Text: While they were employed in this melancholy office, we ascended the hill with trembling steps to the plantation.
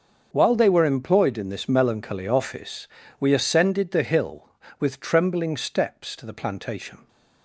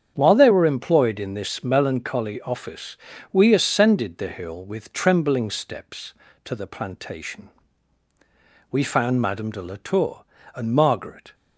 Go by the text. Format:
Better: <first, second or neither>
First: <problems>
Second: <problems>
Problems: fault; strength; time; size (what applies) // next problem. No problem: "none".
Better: first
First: starts louder than the rest; until 1.3 s; 6.5 dB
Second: starts louder than the rest; strong; until 1.1 s; 8 dB // goes on to say "We found Madame de la Tour and Margaret"; strong; from 8.6 s on; 2.6 s long